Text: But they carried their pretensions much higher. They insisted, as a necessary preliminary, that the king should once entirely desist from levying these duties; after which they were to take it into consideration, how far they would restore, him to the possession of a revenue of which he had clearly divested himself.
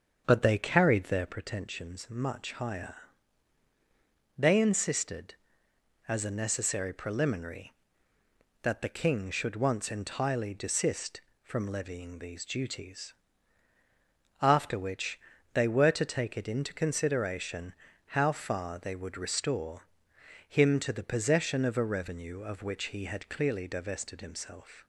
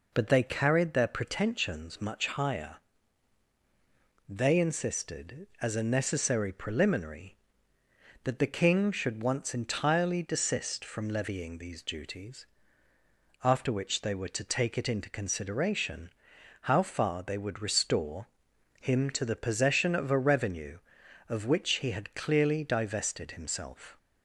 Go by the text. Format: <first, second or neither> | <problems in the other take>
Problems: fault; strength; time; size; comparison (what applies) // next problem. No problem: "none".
second | starts louder than the rest; until 1.4 s; 7 dB // pauses between "which" and "they"; slight; at 15.1 s; 0.34 s long